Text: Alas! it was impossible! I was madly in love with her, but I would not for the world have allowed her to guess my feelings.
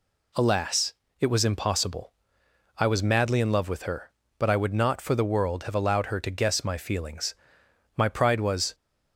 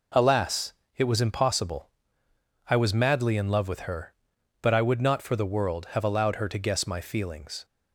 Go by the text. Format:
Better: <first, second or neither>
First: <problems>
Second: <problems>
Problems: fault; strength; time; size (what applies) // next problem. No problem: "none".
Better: second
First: goes on to say "My pride was"; noticeable; from 7.9 s on; 0.78 s long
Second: none